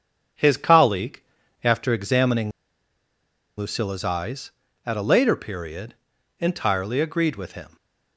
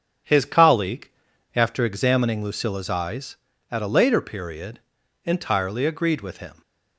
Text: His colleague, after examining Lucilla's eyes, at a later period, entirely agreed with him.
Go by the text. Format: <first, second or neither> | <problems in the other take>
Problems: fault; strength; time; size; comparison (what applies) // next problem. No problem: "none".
second | starts louder than the rest; strong; until 1.8 s; 8.5 dB; strong in the second // pauses between "examining" and "Lucilla's"; at 2.5 s; 1.0 s long